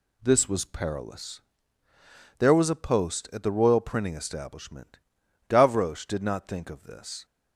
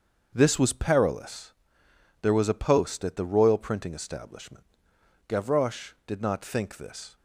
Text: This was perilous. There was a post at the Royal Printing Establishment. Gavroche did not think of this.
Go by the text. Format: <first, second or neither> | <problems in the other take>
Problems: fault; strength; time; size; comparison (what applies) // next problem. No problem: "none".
first | starts louder than the rest; until 1.3 s; 6.5 dB // skips "of"; at 6.7 s